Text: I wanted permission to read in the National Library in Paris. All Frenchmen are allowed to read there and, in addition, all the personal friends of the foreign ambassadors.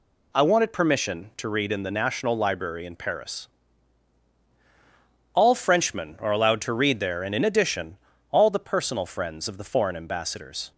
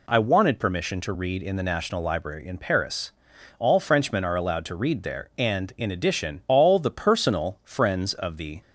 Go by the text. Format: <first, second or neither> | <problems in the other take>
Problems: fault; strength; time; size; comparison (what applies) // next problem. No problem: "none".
first | stops before "foreign ambassadors"; at 8.6 s